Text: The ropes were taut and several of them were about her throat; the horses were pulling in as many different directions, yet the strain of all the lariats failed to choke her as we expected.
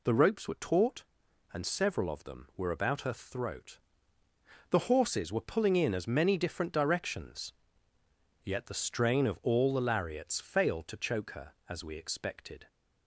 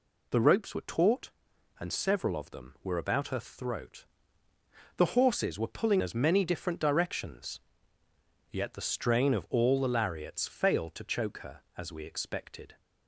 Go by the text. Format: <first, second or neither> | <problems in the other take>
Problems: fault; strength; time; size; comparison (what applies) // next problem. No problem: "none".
first | skips "in"; at 6.0 s